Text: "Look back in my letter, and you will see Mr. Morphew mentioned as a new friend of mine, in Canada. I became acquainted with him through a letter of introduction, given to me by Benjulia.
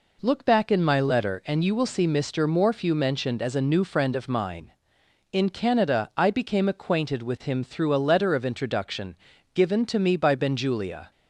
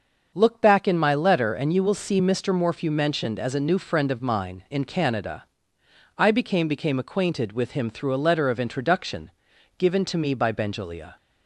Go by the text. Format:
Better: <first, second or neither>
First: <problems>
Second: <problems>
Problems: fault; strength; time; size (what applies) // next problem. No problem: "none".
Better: first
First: none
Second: starts louder than the rest; until 1.3 s; 6.5 dB // says "became" twice; at 6.6 s